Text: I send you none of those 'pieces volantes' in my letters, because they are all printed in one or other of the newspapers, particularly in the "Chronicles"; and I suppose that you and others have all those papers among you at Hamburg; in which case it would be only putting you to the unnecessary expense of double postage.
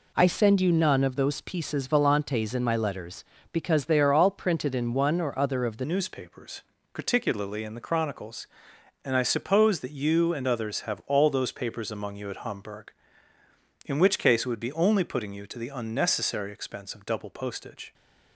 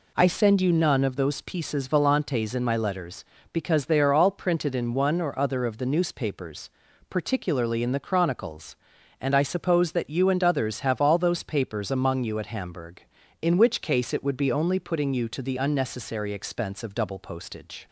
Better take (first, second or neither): second